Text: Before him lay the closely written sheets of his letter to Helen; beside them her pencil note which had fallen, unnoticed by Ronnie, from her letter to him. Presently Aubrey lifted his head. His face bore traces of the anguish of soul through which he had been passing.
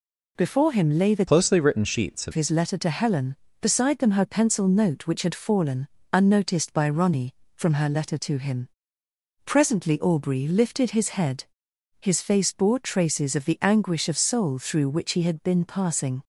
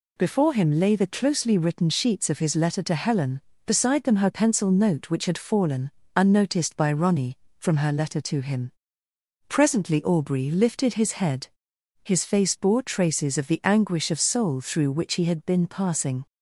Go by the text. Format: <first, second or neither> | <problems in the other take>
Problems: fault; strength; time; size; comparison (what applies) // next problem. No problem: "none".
second | changes voice from "closely" to "of"; from 1.2 to 2.3 s; 1.1 s long